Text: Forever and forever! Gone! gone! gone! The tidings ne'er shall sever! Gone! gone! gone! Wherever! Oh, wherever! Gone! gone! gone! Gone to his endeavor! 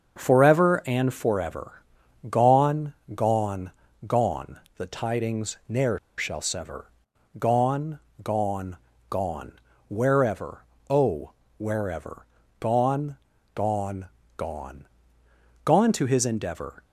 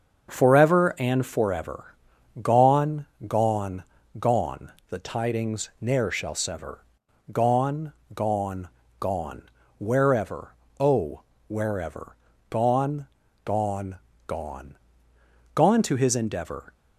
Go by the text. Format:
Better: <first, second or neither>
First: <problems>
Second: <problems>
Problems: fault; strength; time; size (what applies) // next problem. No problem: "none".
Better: second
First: starts louder than the rest; until 1.2 s; 6.5 dB // pauses between "ne'er" and "shall"; slight; at 5.9 s; 0.19 s long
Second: starts louder than the rest; until 1.3 s; 6.5 dB